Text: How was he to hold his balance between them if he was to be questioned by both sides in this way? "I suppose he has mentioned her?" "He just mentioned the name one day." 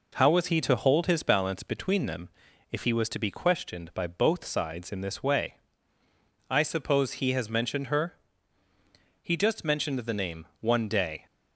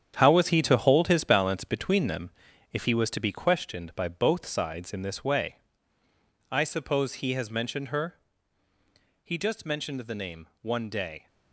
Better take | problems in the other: first | gets quieter; strong; throughout; 10 dB // pauses between "them" and "if"; at 2.3 s; 0.40 s long; also in the first

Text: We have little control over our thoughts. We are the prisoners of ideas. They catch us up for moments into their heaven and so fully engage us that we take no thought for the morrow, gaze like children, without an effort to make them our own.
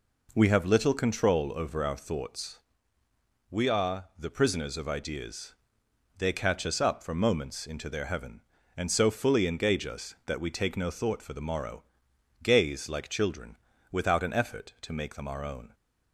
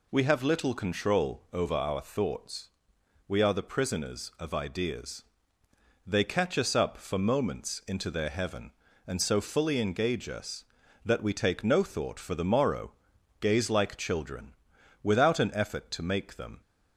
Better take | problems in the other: first | stops before "our own"; at 16.6 s

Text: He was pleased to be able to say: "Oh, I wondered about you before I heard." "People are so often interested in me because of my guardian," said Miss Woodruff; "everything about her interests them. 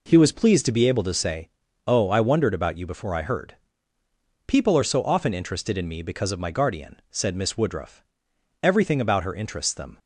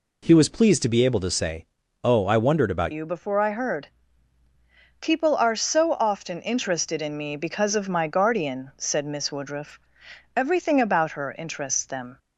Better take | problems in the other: first | changes voice at "you"; from 2.9 s on; 9.2 s long

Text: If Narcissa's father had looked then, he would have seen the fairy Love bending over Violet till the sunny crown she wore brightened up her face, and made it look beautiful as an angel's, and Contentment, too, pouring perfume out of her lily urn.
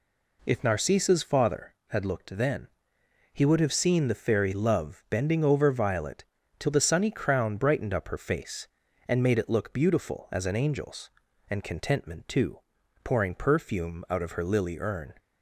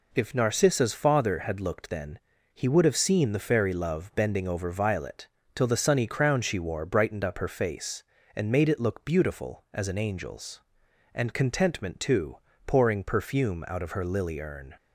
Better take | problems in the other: second | pauses between "Violet" and "till"; slight; at 6.2 s; 0.34 s long; slight in the second // skips "she wore"; at 7.5 s

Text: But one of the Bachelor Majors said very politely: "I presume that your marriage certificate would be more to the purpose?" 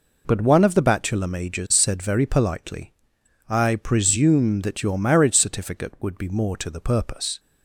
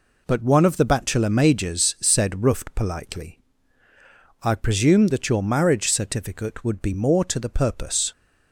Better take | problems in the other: first | says "ruft" for "very"; at 2.4 s

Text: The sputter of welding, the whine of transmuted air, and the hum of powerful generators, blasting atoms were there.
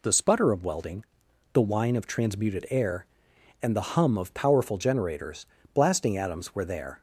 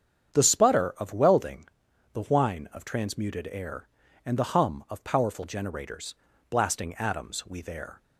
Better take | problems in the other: first | starts louder than the rest; strong; until 1.3 s; 8 dB // says "we" for "were"; at 7.4 s

